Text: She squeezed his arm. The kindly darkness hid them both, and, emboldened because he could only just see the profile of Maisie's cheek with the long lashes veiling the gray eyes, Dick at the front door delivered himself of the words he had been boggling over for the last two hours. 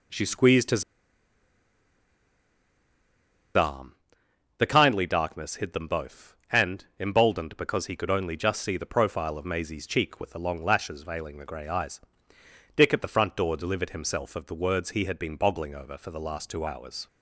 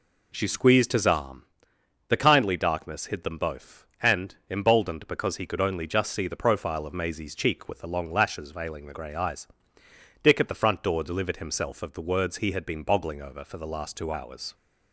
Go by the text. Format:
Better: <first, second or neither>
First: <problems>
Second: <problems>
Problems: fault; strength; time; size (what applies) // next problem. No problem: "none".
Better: second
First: pauses between "his" and "arm"; strong; at 0.8 s; 2.7 s long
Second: none